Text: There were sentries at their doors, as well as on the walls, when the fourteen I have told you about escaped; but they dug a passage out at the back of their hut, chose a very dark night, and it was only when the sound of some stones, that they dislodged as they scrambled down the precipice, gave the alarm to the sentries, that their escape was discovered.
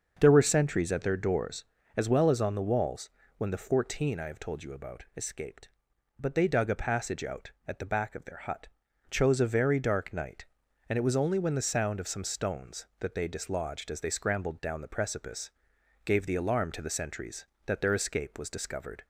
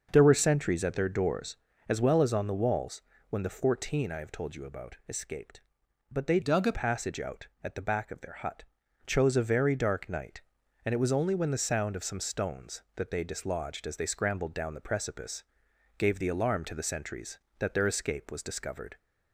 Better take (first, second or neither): first